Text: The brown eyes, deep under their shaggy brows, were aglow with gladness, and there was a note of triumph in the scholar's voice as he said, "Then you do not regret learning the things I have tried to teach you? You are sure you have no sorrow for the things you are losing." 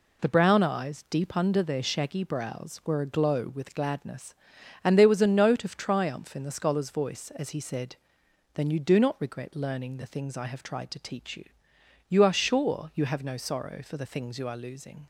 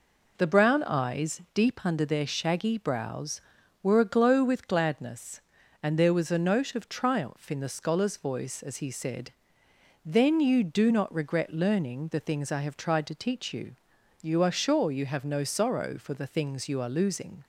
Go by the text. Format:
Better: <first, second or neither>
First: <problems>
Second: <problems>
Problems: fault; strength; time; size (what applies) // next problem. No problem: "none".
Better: neither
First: none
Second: none